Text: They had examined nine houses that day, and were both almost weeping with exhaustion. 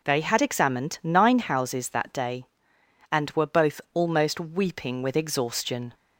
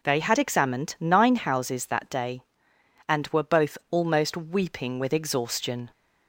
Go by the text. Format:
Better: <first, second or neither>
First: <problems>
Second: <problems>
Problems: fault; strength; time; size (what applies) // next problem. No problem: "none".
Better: neither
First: none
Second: none